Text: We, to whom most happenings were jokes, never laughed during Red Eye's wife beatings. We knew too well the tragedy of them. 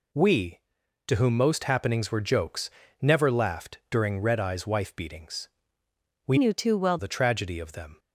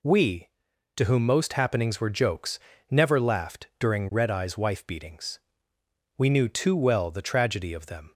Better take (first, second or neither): second